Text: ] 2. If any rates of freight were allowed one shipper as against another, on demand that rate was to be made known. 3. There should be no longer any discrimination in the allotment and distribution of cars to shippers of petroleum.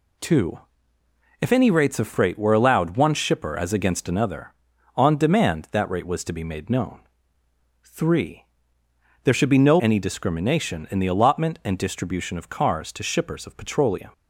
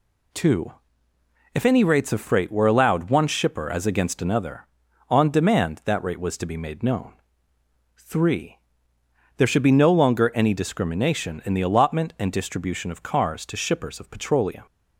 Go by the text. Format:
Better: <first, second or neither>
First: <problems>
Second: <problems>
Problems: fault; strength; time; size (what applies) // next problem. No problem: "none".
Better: second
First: skips "longer"; at 9.7 s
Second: none